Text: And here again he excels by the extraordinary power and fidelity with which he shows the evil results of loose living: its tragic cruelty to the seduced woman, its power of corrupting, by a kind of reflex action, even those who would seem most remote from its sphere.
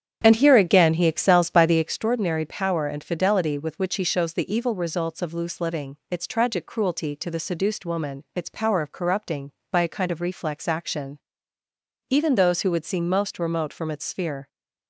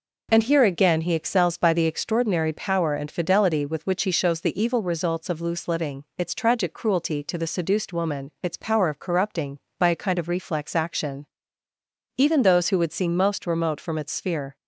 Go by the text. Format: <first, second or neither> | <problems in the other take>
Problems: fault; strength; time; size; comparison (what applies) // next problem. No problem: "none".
second | starts louder than the rest; strong; until 2.0 s; 8.5 dB